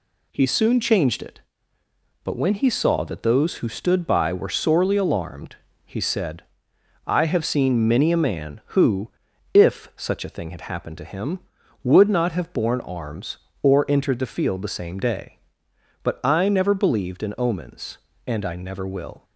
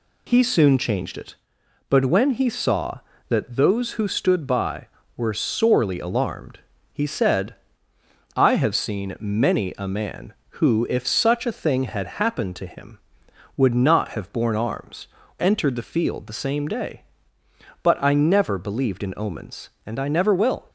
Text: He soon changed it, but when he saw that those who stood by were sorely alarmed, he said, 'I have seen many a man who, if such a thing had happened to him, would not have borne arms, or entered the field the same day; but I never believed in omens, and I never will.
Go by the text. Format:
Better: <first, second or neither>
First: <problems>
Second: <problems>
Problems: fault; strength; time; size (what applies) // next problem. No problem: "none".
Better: first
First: none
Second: skips "or"; at 15.2 s